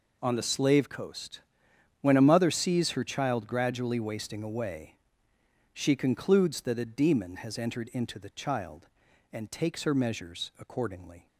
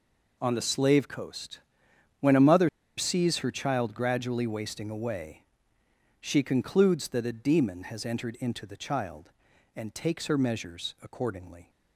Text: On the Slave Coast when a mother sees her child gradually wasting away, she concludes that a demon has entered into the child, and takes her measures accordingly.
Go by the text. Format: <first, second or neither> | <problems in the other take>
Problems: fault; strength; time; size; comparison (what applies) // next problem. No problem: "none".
first | pauses between "Coast" and "when"; noticeable; at 1.5 s; 0.60 s long; noticeable in the first // pauses between "mother" and "sees"; slight; at 2.6 s; 0.28 s long